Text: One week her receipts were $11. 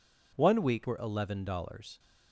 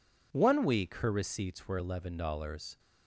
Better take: second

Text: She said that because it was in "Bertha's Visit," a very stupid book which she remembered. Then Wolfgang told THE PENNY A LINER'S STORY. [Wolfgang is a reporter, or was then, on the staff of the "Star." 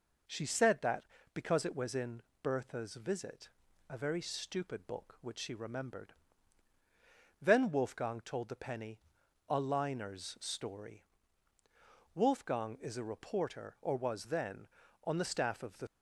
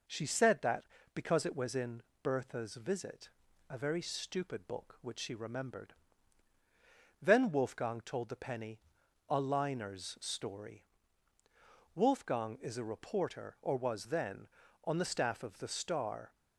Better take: second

